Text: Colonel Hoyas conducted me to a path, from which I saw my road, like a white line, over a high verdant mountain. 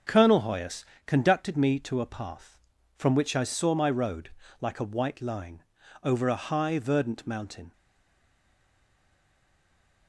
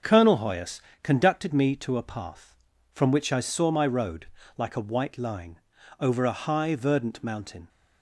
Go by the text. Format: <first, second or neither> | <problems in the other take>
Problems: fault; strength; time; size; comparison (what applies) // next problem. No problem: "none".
second | starts louder than the rest; until 1.2 s; 6.5 dB; also in the second // pauses between "Hoyas" and "conducted"; slight; at 0.8 s; 0.20 s long; slight in the second // stays silent after the last word; from 7.7 s on; 2.3 s long